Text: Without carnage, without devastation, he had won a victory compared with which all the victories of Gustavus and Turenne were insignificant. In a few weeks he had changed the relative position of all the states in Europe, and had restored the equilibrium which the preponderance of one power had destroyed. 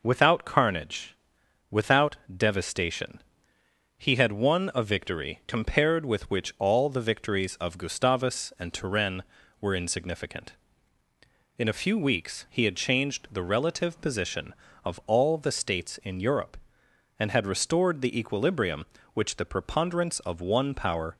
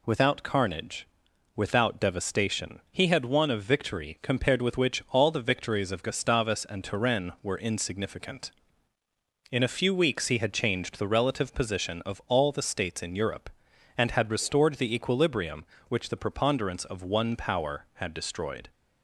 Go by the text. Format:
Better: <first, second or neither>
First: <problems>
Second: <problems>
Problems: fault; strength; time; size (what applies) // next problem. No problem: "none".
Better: second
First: pauses between "without" and "devastation"; slight; at 2.1 s; 0.20 s long // stops before "had destroyed"; at 21.1 s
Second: none